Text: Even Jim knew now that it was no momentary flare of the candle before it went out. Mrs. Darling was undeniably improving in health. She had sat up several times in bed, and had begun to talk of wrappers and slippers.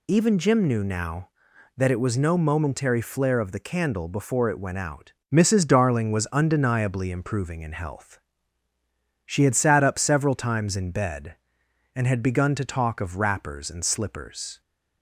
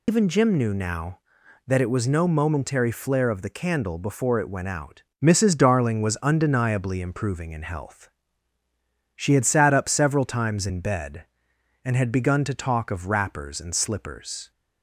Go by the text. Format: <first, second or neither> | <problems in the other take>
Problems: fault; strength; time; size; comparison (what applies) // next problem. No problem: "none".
first | loses the start of "Even"; at 0.0 s; 110 ms